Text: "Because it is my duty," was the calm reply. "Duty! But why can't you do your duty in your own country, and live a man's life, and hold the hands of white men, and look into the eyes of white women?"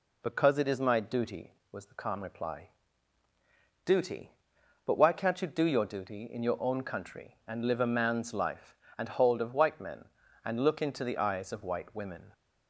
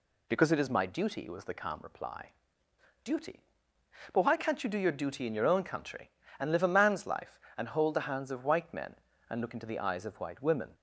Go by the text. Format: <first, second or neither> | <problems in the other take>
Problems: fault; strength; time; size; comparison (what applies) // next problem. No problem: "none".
second | skips "the hands"; at 9.4 s